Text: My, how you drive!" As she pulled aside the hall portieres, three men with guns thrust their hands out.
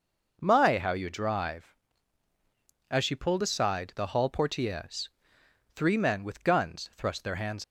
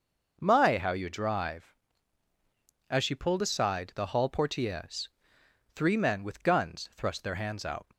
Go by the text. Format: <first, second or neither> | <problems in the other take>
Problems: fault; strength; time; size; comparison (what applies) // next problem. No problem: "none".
second | stops before "out"; at 7.6 s